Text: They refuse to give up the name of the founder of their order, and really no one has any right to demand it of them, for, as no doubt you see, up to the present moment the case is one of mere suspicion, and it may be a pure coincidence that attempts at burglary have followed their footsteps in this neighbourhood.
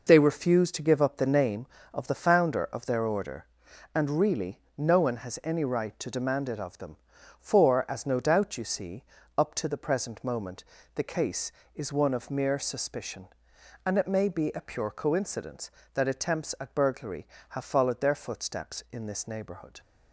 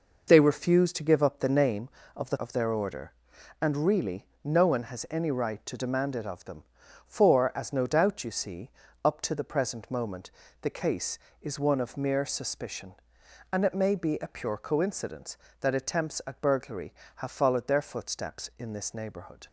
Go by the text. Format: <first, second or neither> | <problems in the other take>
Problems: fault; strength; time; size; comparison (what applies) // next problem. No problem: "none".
first | skips "founder"; at 2.3 s // pauses between "really" and "no"; slight; at 4.2 s; 0.16 s long; slight in the first // pauses between "moment" and "the"; slight; at 10.2 s; 0.32 s long; slight in the first